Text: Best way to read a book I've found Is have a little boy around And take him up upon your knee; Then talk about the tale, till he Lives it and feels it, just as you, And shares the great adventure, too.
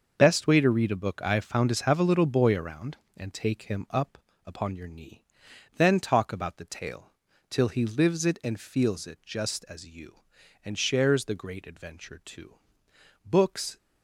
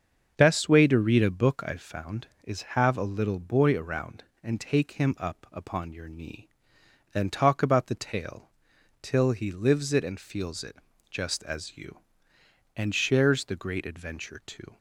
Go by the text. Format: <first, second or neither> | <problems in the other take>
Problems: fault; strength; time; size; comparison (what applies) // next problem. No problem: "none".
second | starts louder than the rest; noticeable; until 1.1 s; 6 dB; also in the second // pauses between "up" and "upon"; slight; at 4.1 s; 0.30 s long // goes on to say "Books"; from 13.2 s on; 0.50 s long